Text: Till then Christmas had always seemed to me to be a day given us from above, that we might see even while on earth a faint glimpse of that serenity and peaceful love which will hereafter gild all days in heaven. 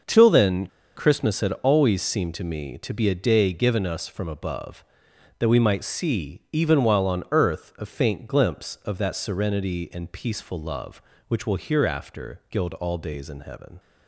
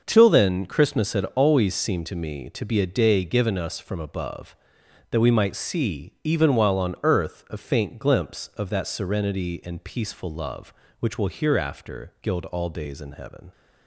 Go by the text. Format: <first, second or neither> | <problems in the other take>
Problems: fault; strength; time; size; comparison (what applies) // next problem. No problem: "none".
second | starts louder than the rest; until 1.3 s; 6 dB; noticeable in the second // pauses between "then" and "Christmas"; slight; at 0.6 s; 0.28 s long